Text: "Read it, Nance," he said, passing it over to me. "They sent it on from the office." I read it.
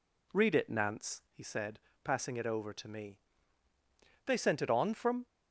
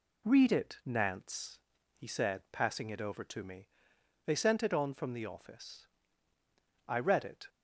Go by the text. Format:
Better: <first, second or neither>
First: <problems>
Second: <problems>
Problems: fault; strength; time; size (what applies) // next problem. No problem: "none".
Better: second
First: stops before "the office I read it"; at 5.2 s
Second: none